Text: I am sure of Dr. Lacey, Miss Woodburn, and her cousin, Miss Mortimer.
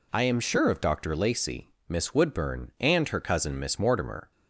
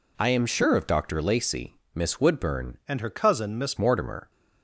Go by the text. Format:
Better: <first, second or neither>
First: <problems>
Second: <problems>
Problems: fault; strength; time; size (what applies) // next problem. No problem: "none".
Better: first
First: none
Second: changes voice from "and" to "Miss"; from 2.8 to 3.7 s; 0.9 s long